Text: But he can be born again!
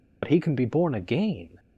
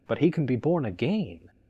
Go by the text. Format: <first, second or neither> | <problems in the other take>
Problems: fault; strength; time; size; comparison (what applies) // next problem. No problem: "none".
second | loses the start of "But"; at 0.2 s; 55 ms